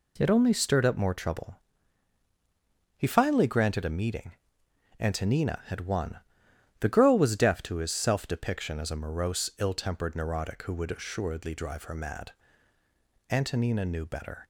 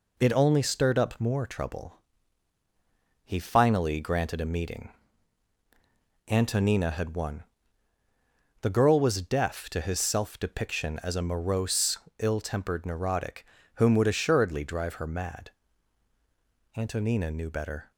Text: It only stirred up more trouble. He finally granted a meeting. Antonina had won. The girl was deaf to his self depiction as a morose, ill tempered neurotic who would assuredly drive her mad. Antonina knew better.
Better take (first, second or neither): first